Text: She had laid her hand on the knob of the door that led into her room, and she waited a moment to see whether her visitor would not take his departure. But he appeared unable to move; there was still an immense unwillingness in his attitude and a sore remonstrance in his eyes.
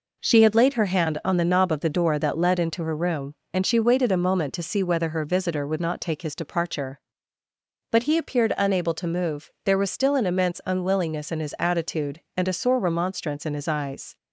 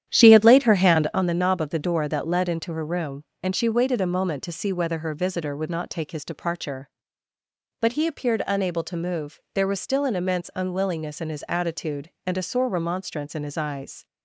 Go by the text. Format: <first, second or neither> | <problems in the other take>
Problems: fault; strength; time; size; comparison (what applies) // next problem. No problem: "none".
first | starts louder than the rest; strong; until 1.2 s; 10 dB